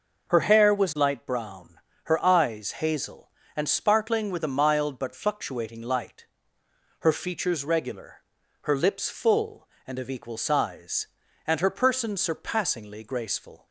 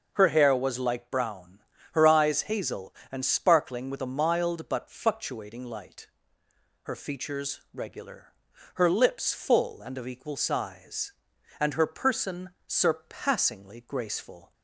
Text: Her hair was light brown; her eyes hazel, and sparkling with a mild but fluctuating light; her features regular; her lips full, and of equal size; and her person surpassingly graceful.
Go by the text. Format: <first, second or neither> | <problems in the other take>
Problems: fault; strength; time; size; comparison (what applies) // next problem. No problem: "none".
neither | none